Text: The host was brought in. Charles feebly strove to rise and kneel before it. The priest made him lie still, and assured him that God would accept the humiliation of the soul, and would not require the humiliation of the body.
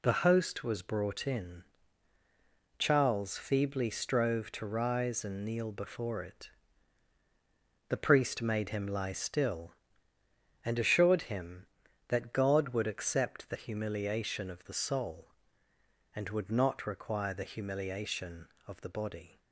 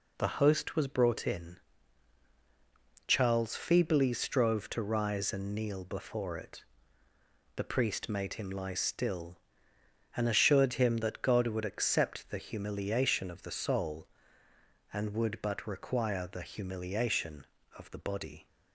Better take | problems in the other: first | says "but" for "not"; at 15.4 s

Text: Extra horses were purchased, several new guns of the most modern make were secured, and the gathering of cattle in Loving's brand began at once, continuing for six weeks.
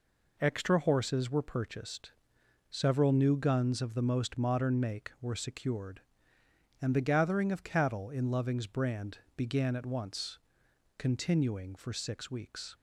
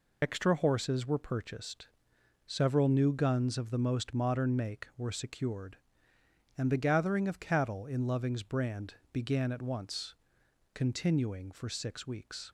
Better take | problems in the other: first | loses the start of "Extra"; at 0.2 s; 65 ms // pauses between "brand" and "began"; slight; at 8.9 s; 0.18 s long; slight in the first

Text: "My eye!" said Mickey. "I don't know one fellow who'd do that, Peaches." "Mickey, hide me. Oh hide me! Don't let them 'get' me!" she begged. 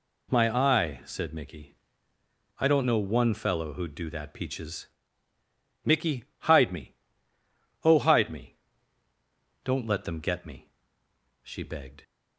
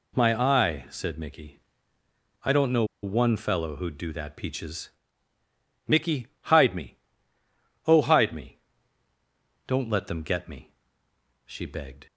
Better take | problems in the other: first | pauses between "know" and "one"; slight; at 2.8 s; 0.18 s long

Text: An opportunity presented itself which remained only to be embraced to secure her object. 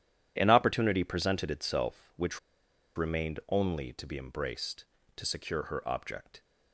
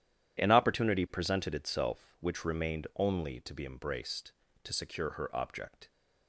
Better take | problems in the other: second | starts louder than the rest; strong; until 1.3 s; 10.5 dB // pauses between "which" and "remained"; noticeable; at 2.3 s; 0.57 s long

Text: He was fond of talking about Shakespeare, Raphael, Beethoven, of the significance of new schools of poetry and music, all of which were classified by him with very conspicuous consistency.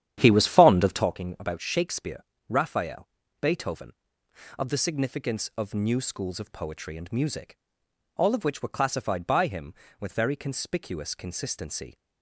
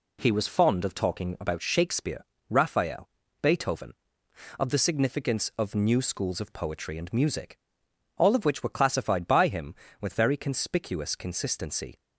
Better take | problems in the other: second | starts louder than the rest; strong; until 1.1 s; 10 dB

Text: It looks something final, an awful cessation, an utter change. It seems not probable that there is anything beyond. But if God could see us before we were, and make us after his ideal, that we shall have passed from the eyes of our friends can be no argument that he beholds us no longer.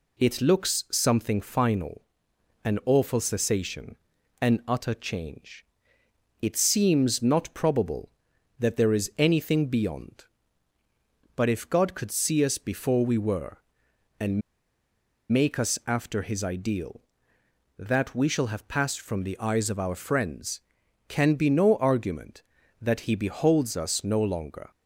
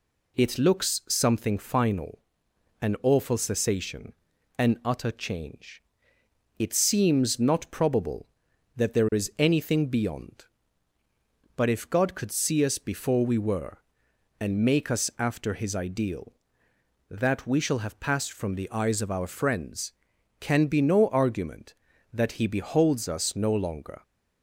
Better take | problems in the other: second | pauses between "and" and "make"; noticeable; at 14.4 s; 0.91 s long

